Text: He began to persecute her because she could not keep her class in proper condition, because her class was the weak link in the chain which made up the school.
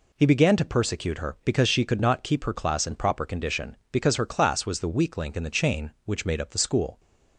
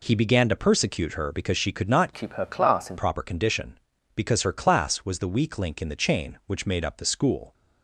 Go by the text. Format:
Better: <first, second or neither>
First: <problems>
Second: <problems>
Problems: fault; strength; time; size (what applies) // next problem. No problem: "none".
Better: first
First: none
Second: changes voice from "keep" to "in"; from 2.1 to 2.9 s; 0.8 s long